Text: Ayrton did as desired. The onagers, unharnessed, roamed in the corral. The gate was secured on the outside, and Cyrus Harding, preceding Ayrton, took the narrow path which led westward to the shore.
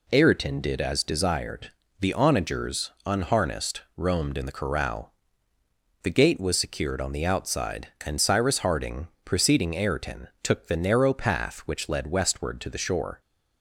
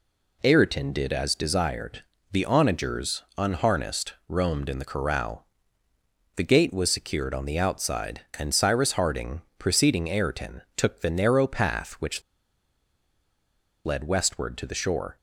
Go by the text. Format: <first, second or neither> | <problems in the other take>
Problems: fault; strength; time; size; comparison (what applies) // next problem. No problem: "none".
first | pauses between "which" and "led"; strong; at 12.2 s; 1.6 s long